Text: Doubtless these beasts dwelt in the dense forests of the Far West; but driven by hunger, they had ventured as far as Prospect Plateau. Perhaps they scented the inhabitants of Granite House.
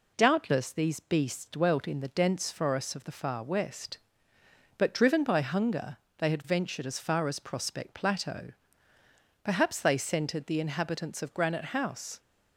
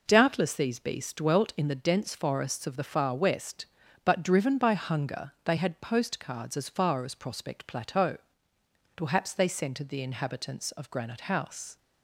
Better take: first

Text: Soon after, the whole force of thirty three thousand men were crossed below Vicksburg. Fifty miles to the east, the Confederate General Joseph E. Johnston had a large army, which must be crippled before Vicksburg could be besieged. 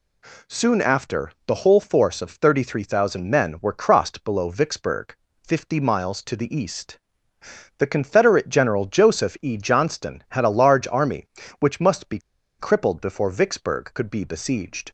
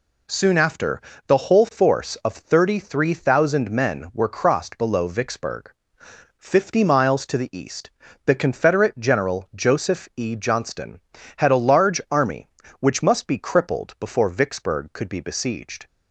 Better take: second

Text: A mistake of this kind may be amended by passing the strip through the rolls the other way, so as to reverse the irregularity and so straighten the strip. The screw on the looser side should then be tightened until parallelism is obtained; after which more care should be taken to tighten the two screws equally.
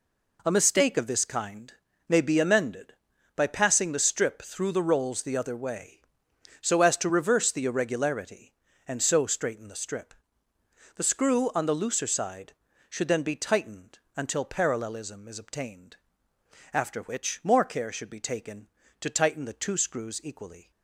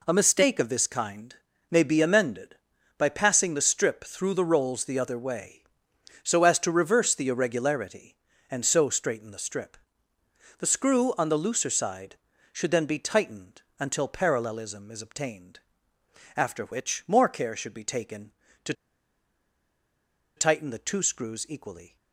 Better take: first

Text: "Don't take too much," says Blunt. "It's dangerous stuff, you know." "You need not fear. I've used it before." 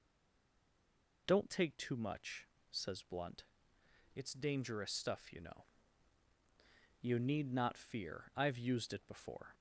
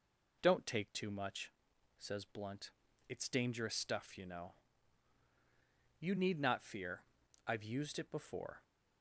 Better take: second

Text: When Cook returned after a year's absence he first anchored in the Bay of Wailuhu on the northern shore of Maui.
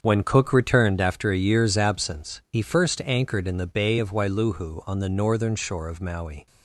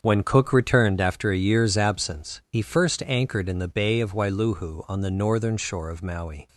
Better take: neither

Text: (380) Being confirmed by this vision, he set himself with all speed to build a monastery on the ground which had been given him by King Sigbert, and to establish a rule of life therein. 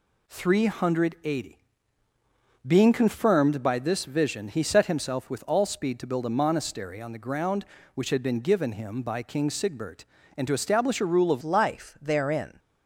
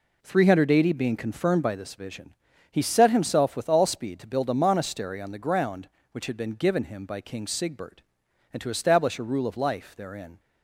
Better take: second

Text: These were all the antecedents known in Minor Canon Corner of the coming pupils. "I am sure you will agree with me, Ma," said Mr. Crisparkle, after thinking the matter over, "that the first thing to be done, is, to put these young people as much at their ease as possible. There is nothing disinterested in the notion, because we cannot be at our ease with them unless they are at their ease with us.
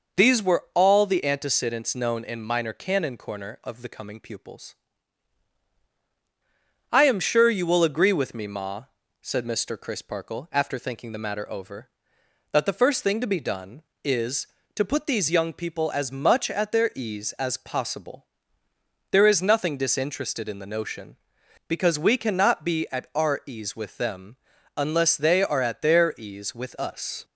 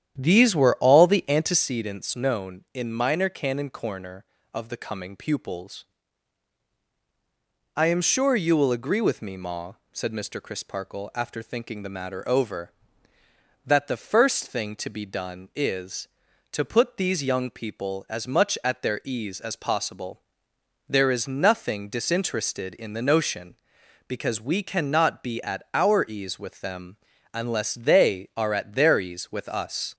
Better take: first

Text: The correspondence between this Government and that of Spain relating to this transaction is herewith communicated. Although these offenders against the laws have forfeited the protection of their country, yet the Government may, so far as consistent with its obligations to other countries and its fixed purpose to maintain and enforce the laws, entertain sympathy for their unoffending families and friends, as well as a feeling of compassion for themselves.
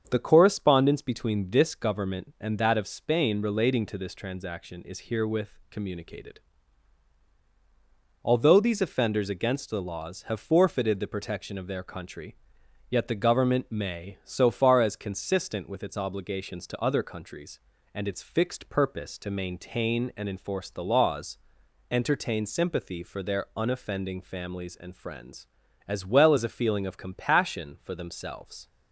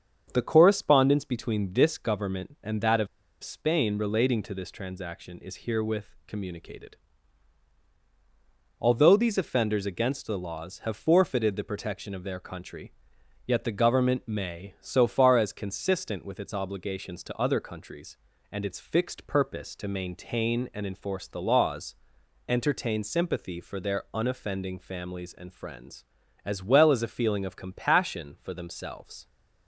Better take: first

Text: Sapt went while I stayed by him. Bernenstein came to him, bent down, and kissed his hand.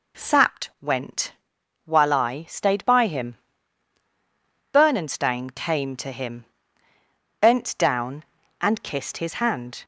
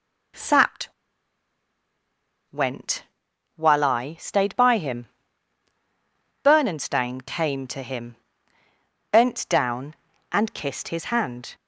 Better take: first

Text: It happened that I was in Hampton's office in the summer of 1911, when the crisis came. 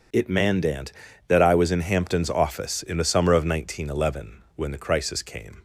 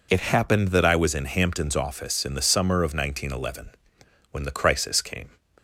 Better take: second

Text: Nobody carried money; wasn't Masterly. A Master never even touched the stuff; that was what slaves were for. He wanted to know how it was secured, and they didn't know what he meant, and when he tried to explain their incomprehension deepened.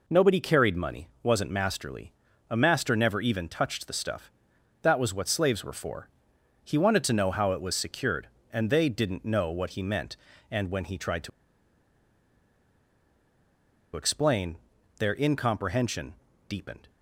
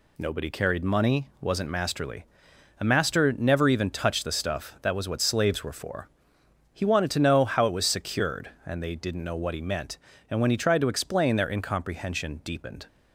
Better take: second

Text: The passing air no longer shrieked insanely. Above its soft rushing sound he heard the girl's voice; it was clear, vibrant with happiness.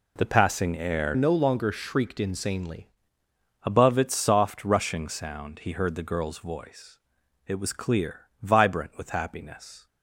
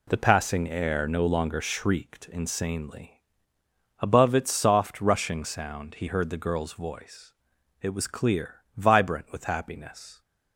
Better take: second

